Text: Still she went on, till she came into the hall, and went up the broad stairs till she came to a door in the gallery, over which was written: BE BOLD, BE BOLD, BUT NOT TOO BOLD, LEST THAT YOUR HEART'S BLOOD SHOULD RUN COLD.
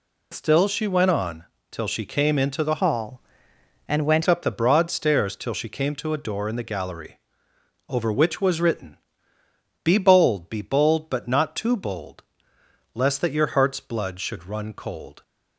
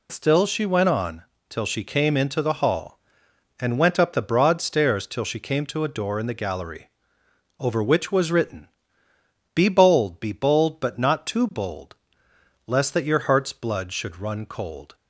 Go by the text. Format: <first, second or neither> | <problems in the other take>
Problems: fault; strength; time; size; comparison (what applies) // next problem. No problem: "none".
second | changes voice from "hall" to "went"; from 2.7 to 4.2 s; 1.5 s long